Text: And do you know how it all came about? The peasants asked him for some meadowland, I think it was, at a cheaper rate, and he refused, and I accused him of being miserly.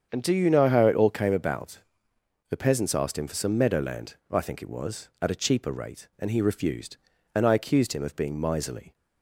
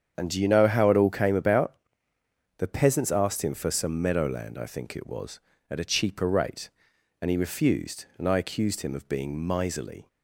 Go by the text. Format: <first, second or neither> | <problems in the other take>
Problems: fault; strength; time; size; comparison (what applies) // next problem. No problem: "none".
neither | starts louder than the rest; strong; the same in both